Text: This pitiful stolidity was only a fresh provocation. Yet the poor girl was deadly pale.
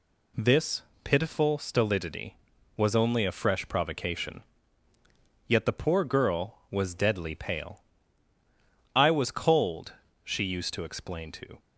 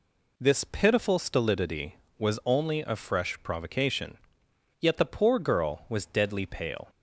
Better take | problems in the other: second | pauses between "This" and "pitiful"; slight; at 0.8 s; 0.24 s long // goes on to say "I was cold she used to explain to"; strong; from 8.9 s on; 2.6 s long

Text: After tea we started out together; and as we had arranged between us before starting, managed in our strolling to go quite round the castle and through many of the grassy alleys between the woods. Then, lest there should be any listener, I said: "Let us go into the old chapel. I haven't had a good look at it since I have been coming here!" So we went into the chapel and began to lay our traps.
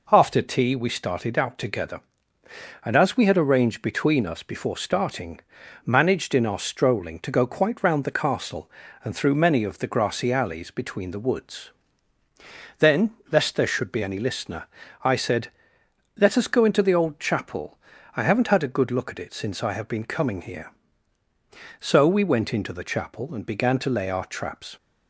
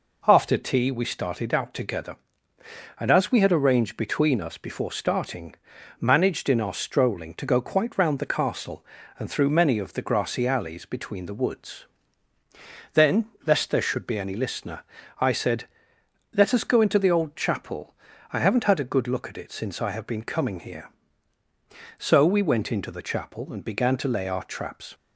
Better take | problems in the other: neither | none

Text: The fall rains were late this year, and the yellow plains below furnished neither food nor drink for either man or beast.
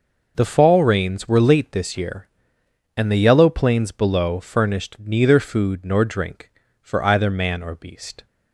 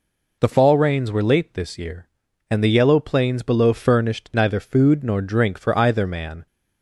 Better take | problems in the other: first | stops before "or beast"; at 6.4 s

